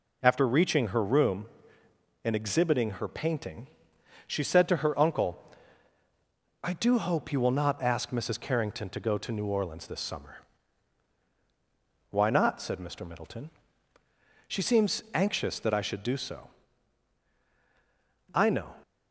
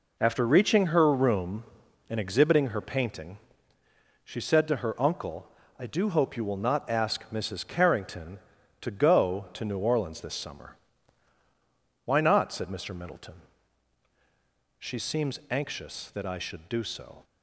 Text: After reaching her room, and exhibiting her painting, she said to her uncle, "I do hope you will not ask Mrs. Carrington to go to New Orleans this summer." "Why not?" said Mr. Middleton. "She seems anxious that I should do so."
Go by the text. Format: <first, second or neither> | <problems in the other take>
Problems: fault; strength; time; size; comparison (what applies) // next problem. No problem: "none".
second | goes on to say "I know"; slight; from 18.3 s on; 0.44 s long